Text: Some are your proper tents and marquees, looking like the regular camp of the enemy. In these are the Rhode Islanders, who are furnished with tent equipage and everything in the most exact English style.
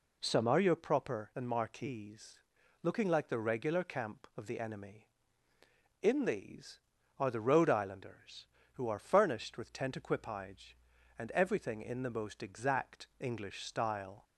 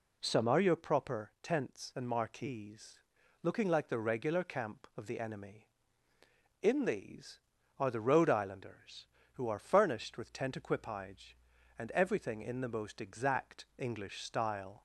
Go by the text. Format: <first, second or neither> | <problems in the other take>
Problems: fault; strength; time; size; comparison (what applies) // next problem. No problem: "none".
second | skips "tents"; at 1.3 s